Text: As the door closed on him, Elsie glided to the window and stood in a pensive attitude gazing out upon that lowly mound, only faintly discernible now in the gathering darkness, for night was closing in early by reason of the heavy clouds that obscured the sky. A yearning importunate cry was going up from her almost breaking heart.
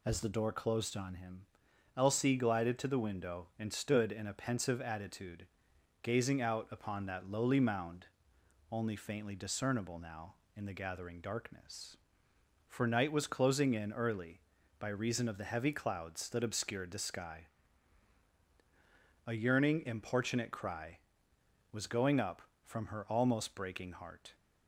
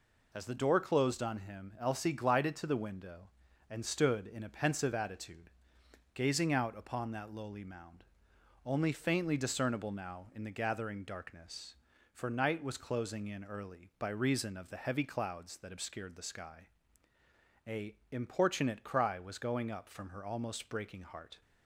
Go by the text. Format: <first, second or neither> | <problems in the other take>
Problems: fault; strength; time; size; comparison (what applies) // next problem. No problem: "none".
first | pauses between "attitude" and "gazing"; noticeable; at 5.5 s; 0.62 s long; noticeable in the first // skips "yearning"; at 18.0 s